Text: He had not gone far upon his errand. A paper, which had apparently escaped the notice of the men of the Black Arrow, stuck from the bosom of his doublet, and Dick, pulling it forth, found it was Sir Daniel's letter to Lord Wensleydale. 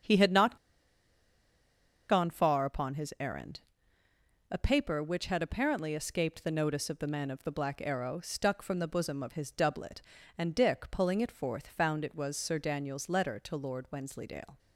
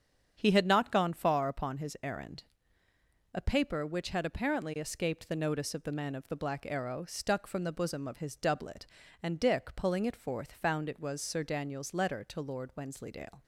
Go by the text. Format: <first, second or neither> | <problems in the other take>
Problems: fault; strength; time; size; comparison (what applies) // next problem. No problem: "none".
second | starts louder than the rest; strong; until 2.5 s; 8 dB; strong in the second // pauses between "not" and "gone"; strong; at 0.5 s; 1.5 s long